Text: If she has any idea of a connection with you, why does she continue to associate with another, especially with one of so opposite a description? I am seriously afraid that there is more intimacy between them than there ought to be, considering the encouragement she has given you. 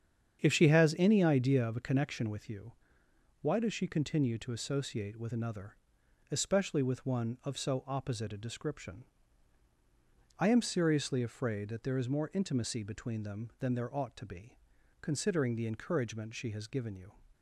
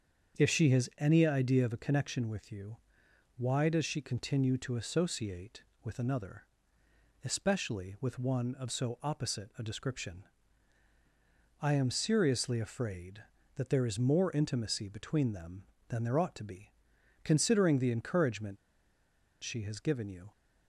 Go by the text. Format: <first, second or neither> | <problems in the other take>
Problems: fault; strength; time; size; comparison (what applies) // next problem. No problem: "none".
first | starts louder than the rest; until 1.4 s; 7 dB; strong in the first // pauses between "encouragement" and "she"; noticeable; at 18.5 s; 0.86 s long